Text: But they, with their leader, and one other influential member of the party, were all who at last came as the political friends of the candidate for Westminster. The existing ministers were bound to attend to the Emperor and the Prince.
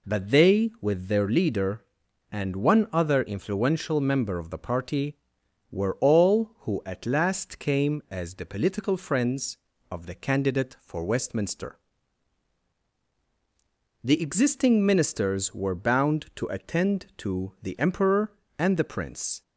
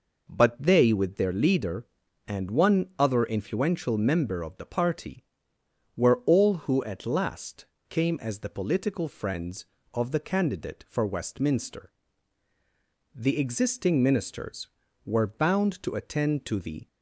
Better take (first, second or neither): first